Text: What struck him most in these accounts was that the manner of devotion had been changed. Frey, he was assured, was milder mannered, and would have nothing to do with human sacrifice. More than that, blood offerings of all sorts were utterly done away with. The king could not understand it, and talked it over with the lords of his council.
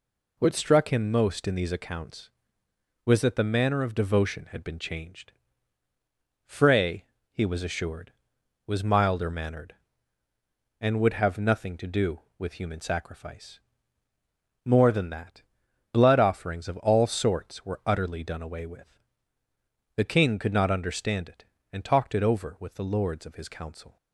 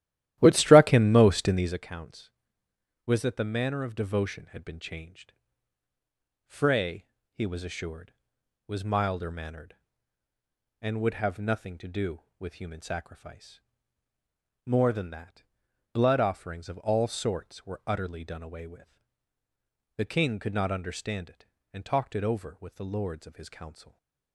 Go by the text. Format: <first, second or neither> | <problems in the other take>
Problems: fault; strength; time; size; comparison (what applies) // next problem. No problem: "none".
first | starts louder than the rest; strong; until 1.8 s; 13.5 dB // stays silent after the last word; slight; from 23.8 s on; 0.5 s long